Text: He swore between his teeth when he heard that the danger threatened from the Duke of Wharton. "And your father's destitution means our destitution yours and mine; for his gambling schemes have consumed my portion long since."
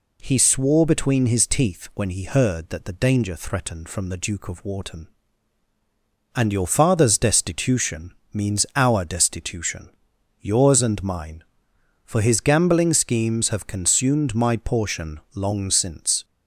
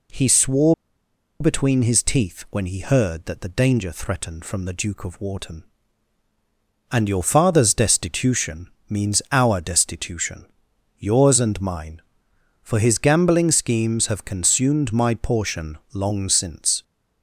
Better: first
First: pauses between "destitution" and "means"; slight; at 8.1 s; 0.20 s long // pauses between "destitution" and "yours"; noticeable; at 9.8 s; 0.52 s long // pauses between "portion" and "long"; slight; at 15.2 s; 0.15 s long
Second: pauses between "swore" and "between"; noticeable; at 0.7 s; 0.66 s long // pauses between "destitution" and "means"; slight; at 8.6 s; 0.20 s long // pauses between "destitution" and "yours"; noticeable; at 10.4 s; 0.54 s long // pauses between "portion" and "long"; slight; at 15.7 s; 0.16 s long

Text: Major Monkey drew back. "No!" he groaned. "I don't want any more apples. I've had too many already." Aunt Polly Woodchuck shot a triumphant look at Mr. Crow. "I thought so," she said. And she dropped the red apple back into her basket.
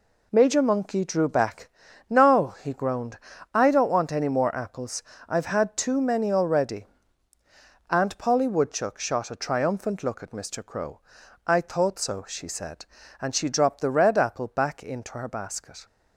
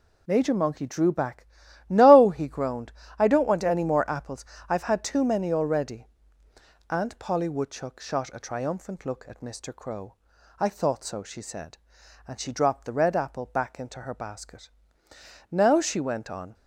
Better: first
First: none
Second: goes on to say "Now she went on"; noticeable; from 15.5 s on; 1.0 s long

